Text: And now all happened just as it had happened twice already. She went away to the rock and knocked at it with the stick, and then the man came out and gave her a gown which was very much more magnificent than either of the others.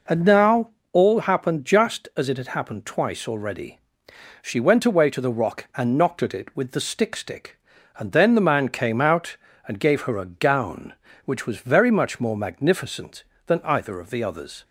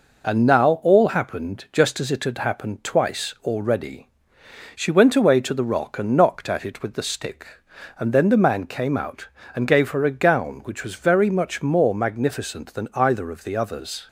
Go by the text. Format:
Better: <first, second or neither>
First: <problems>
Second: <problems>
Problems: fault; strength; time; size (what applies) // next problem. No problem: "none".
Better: second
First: pauses between "now" and "all"; slight; at 0.6 s; 0.24 s long // says "stick" twice; at 7.1 s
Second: none